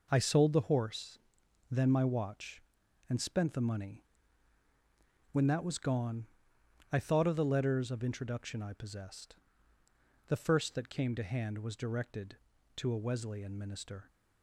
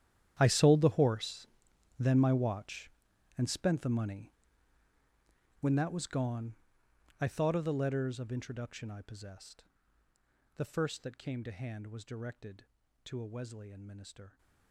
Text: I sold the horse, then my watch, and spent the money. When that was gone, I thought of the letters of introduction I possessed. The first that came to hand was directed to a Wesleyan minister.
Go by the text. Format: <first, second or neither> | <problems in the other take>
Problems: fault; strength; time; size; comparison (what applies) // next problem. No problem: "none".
first | gets quieter; strong; throughout; 18 dB